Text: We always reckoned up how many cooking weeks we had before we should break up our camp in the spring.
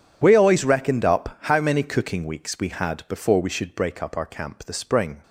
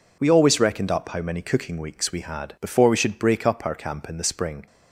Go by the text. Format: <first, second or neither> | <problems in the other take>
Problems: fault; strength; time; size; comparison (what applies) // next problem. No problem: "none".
second | skips "in"; at 4.6 s